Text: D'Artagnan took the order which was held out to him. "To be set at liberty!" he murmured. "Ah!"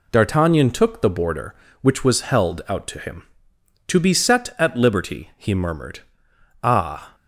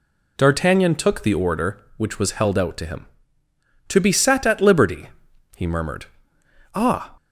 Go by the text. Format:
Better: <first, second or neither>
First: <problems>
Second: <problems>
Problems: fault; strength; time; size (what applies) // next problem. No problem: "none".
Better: second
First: says "border" for "order"; at 1.1 s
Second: none